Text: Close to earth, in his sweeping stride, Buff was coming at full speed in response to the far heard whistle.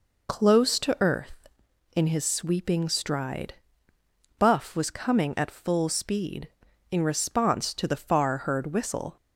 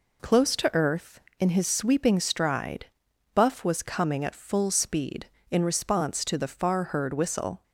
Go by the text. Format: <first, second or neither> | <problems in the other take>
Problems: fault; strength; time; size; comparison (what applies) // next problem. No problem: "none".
neither | none